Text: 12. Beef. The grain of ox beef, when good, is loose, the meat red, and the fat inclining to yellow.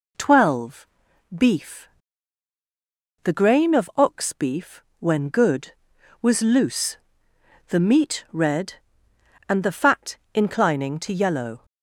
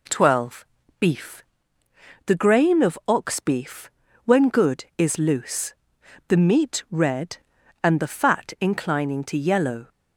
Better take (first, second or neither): second